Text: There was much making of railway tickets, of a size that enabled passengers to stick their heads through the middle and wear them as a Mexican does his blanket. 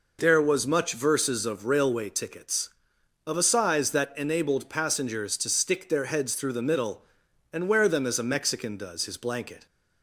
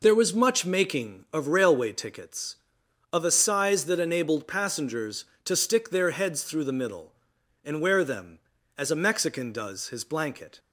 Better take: second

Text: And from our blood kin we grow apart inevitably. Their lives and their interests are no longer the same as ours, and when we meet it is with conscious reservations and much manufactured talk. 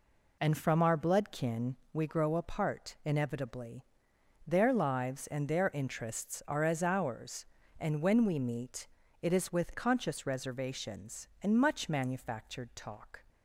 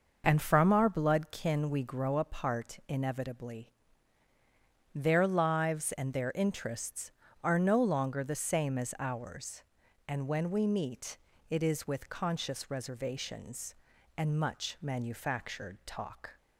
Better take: second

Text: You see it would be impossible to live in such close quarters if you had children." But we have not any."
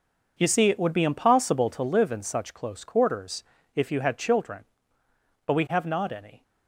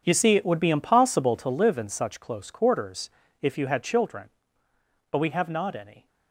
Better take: first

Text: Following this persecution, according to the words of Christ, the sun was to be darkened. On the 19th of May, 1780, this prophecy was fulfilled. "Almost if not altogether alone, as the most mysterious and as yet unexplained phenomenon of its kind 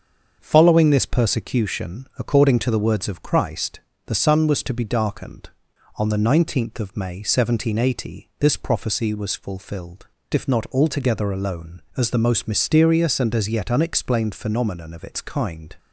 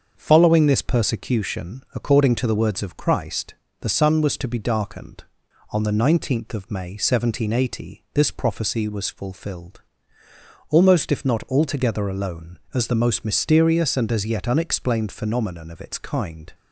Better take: second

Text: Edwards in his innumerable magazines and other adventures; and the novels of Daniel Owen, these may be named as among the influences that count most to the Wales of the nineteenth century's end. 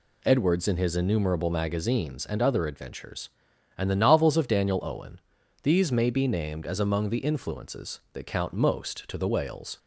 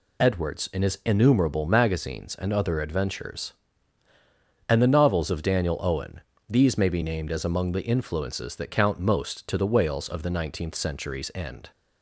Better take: second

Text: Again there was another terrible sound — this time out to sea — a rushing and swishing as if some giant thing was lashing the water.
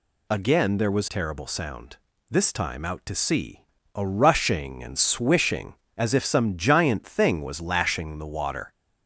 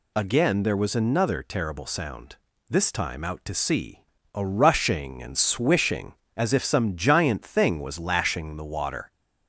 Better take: second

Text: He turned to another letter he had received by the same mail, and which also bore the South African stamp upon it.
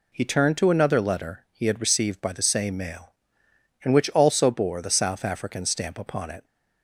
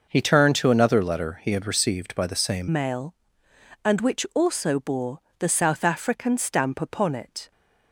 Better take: first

